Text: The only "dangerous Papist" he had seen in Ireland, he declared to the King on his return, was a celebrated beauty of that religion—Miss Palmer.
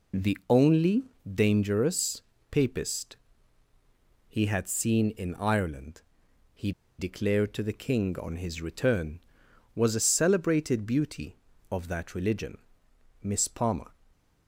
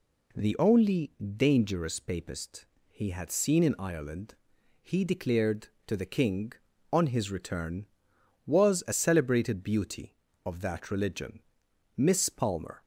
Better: second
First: pauses between "only" and "dangerous"; slight; at 1.0 s; 0.16 s long // pauses between "dangerous" and "Papist"; slight; at 2.2 s; 0.28 s long // pauses between "Papist" and "he"; at 3.1 s; 1.1 s long // pauses between "he" and "declared"; slight; at 6.7 s; 0.27 s long // stays silent after the last word; slight; from 13.9 s on; 0.5 s long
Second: pauses between "Papist" and "he"; slight; at 2.6 s; 0.22 s long

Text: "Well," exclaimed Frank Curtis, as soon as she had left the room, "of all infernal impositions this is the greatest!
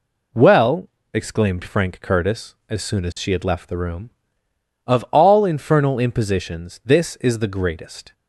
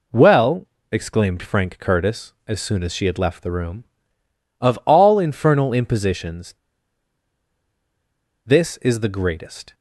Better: first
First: none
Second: pauses between "impositions" and "this"; strong; at 6.5 s; 1.9 s long

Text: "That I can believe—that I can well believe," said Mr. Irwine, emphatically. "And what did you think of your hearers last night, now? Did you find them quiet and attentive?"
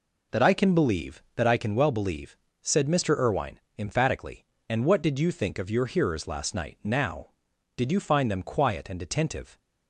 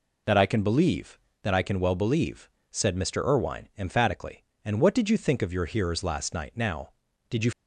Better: first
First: none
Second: stops before "find them quiet and attentive"; at 7.5 s

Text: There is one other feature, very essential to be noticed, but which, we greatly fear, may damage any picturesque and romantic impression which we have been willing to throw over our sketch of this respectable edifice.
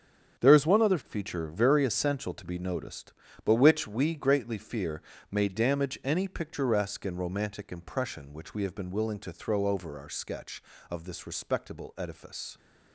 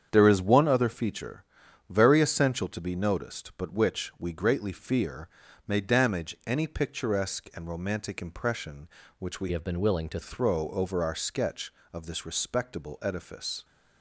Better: first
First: starts louder than the rest; strong; until 1.4 s; 7.5 dB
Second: starts louder than the rest; strong; until 1.1 s; 8 dB // changes voice from "have" to "to"; from 9.5 to 10.1 s; 0.6 s long

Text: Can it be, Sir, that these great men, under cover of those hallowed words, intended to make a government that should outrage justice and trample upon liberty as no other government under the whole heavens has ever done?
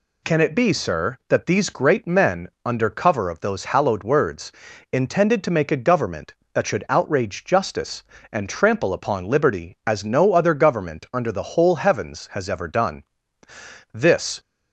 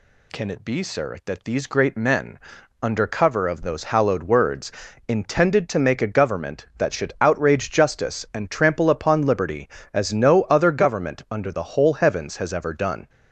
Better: second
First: goes on to say "This"; slight; from 13.9 s on; 0.48 s long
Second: none

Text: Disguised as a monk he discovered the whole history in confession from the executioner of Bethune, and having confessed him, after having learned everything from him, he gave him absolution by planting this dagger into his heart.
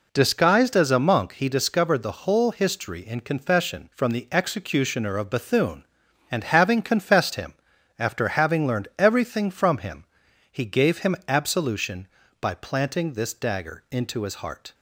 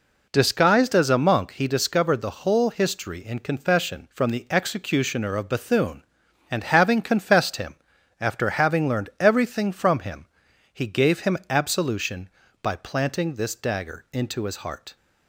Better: neither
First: none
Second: none

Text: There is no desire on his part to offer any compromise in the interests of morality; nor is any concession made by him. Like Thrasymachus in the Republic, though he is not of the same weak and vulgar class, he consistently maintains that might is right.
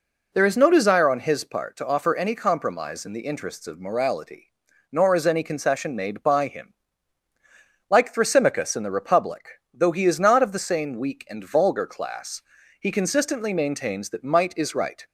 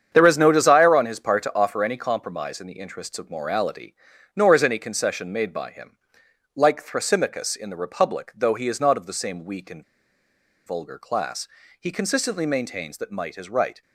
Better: first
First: none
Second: starts louder than the rest; strong; until 1.1 s; 8 dB // pauses between "and" and "vulgar"; noticeable; at 9.8 s; 0.83 s long

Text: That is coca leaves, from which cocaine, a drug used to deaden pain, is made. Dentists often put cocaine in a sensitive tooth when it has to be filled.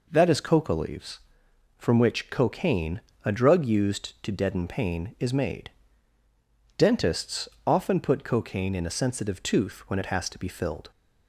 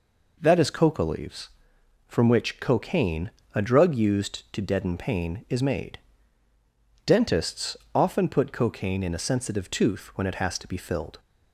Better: neither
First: pauses between "Dentists" and "often"; slight; at 7.4 s; 0.18 s long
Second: pauses between "Dentists" and "often"; slight; at 7.7 s; 0.18 s long

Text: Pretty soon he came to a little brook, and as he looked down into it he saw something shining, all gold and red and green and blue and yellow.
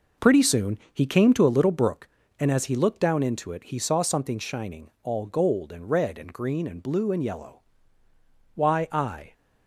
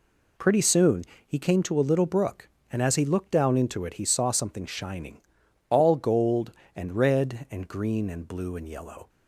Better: second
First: pauses between "soon" and "he"; slight; at 0.7 s; 0.16 s long // goes on to say "Why I"; noticeable; from 8.5 s on; 0.78 s long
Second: pauses between "soon" and "he"; slight; at 1.0 s; 0.24 s long

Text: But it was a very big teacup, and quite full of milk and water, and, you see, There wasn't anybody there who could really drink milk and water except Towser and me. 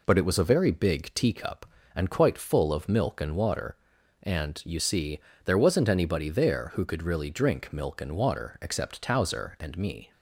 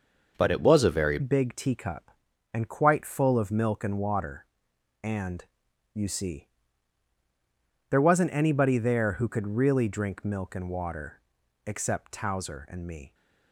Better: first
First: none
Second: starts louder than the rest; noticeable; until 1.3 s; 6 dB // changes voice at "big"; from 1.1 s on; 12.0 s long // pauses between "water" and "except"; at 11.2 s; 0.44 s long

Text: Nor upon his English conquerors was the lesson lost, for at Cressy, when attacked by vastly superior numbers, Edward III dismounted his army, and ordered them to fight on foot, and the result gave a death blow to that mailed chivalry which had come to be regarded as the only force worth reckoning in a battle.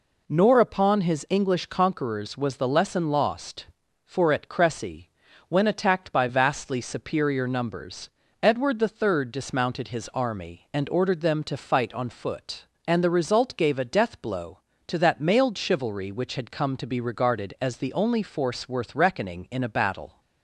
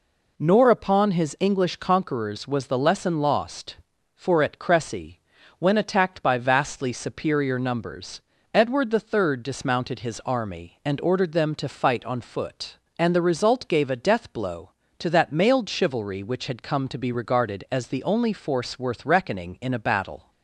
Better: neither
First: none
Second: none

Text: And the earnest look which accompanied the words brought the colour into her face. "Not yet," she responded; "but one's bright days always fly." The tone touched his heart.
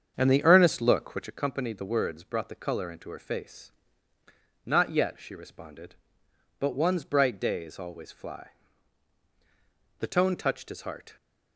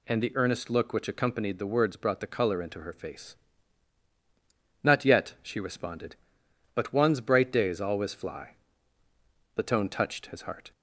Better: second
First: starts louder than the rest; strong; until 1.4 s; 7.5 dB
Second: none

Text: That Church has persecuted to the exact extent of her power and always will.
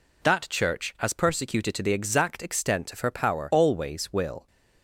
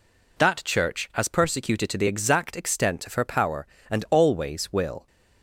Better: second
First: skips "and"; at 3.5 s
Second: none

